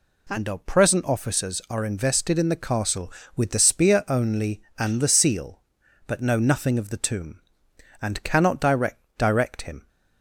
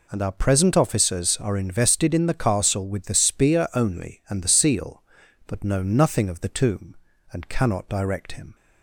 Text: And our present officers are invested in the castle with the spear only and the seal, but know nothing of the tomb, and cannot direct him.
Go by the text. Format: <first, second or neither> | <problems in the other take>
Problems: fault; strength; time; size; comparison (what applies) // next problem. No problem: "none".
second | says "direct" twice; at 9.1 s